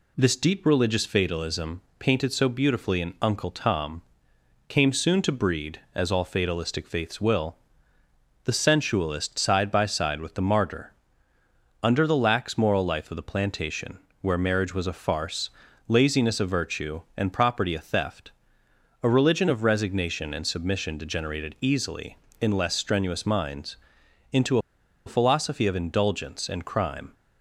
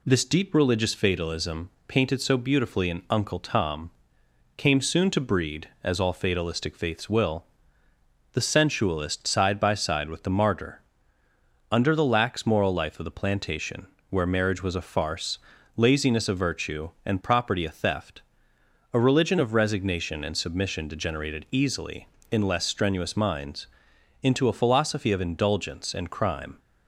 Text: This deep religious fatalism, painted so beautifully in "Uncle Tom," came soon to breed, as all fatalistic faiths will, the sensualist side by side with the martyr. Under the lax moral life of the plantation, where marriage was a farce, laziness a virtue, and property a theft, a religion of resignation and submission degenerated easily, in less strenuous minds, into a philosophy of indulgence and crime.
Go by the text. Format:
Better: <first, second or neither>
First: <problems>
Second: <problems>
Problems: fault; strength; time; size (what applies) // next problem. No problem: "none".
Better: second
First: pauses between "into" and "a"; noticeable; at 24.5 s; 0.47 s long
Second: none